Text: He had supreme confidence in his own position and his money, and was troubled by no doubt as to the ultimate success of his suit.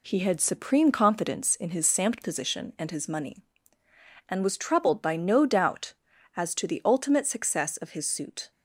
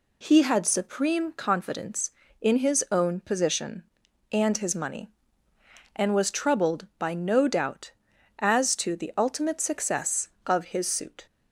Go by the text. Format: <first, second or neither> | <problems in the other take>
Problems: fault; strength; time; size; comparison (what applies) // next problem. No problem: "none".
second | says "samt" for "own"; at 1.8 s